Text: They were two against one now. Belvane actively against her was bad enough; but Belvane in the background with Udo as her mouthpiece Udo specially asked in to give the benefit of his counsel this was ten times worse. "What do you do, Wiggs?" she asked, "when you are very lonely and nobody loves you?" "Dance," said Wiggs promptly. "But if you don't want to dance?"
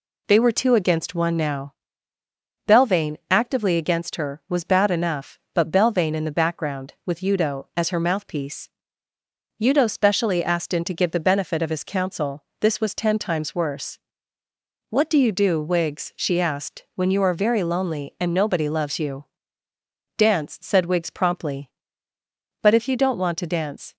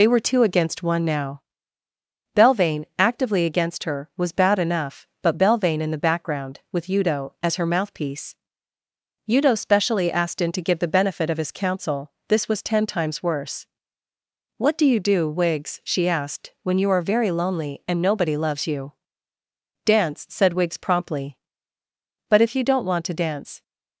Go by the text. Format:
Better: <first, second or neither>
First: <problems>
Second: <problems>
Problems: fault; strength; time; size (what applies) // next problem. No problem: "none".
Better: first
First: pauses between "mouthpiece" and "Udo"; noticeable; at 8.6 s; 0.94 s long // pauses between "counsel" and "this"; slight; at 12.4 s; 0.16 s long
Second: loses the start of "They"; at 0.0 s; 55 ms // pauses between "mouthpiece" and "Udo"; noticeable; at 8.3 s; 0.96 s long // pauses between "counsel" and "this"; slight; at 12.1 s; 0.16 s long